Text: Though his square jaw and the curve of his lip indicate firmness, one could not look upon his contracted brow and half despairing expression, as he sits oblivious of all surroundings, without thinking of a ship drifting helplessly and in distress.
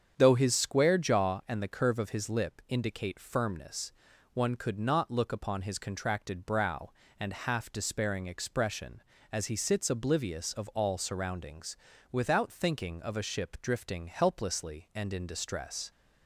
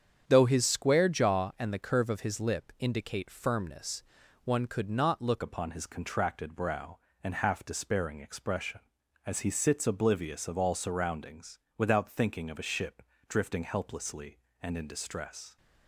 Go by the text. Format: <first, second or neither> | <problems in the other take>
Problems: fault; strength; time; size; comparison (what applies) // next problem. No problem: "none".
first | starts louder than the rest; strong; until 1.2 s; 8 dB; strong in the first // changes voice at "upon"; from 5.4 s on; 10.1 s long // pauses between "ship" and "drifting"; slight; at 13.0 s; 0.26 s long